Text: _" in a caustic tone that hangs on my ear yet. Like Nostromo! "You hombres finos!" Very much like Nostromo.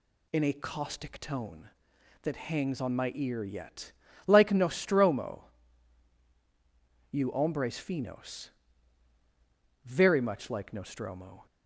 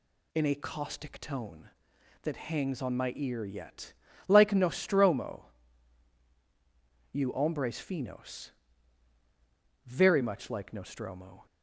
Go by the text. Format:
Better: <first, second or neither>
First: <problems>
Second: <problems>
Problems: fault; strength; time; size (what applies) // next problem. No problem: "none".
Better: neither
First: none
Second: none